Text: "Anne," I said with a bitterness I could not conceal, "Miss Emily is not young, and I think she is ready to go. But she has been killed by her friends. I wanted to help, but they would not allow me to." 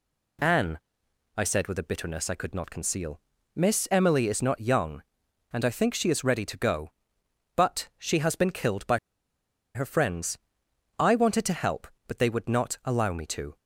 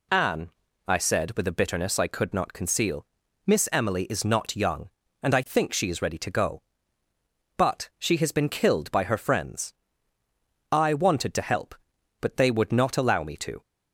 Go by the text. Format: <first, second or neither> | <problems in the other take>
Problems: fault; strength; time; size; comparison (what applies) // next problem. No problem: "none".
second | pauses between "by" and "her"; noticeable; at 8.9 s; 0.77 s long